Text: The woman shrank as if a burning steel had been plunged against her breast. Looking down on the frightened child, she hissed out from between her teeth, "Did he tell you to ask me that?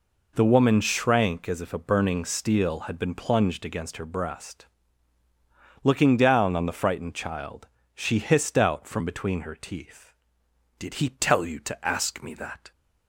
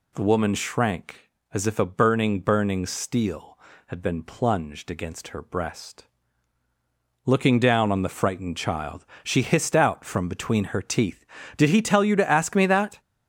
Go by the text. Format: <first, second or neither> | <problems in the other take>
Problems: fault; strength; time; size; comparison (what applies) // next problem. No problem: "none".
first | says "burning" twice; at 2.3 s